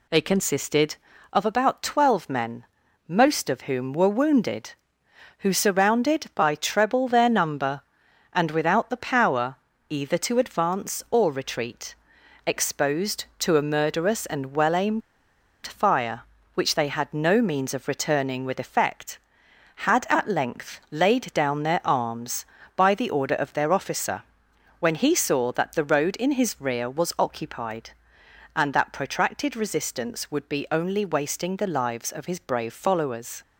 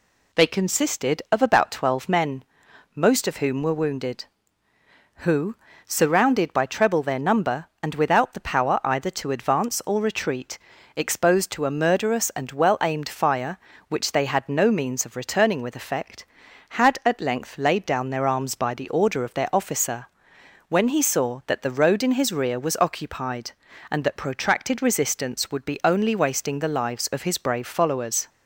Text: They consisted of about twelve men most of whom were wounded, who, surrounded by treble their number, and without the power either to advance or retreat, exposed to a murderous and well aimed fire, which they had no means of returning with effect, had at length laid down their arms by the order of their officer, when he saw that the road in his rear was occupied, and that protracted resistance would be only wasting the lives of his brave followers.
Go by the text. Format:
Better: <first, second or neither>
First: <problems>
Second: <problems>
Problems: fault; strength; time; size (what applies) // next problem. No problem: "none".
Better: second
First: pauses between "men" and "most"; at 2.6 s; 0.40 s long // pauses between "power" and "either"; slight; at 9.5 s; 0.34 s long // pauses between "aimed" and "fire"; noticeable; at 15.0 s; 0.64 s long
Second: pauses between "men" and "most"; noticeable; at 2.4 s; 0.50 s long